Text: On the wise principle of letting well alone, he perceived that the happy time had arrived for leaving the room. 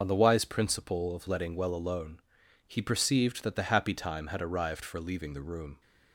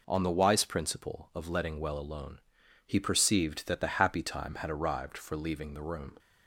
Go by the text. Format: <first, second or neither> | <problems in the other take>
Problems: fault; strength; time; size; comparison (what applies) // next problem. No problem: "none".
second | loses the start of "On"; at 0.0 s; 25 ms